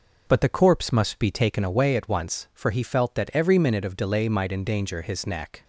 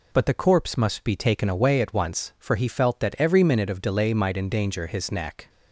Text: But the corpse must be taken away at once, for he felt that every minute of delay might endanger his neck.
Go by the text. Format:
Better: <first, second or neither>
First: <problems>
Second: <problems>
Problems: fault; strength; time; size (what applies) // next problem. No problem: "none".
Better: second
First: starts louder than the rest; noticeable; until 1.5 s; 5 dB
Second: none